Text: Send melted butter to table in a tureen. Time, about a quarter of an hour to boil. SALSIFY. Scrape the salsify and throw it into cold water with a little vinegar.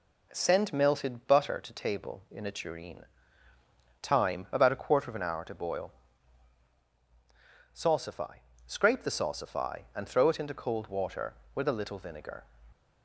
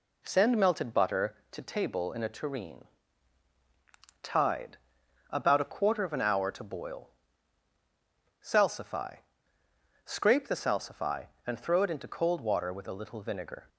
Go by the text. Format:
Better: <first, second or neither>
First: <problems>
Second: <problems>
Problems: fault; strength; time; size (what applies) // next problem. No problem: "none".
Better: first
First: none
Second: says "Tide" for "Time"; at 4.2 s